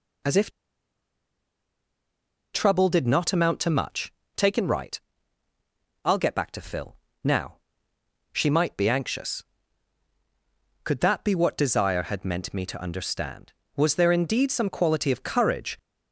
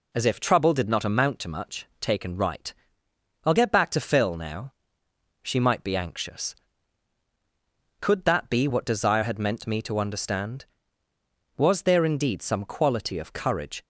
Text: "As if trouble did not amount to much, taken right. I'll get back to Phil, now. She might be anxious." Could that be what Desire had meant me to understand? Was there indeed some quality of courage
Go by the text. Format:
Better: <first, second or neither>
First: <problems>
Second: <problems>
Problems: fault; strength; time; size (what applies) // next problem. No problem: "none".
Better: second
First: pauses between "if" and "trouble"; strong; at 0.5 s; 2.0 s long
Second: none